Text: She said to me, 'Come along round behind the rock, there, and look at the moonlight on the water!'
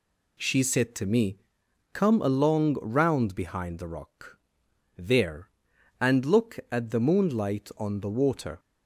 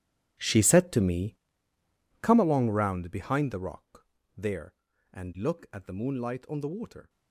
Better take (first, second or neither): first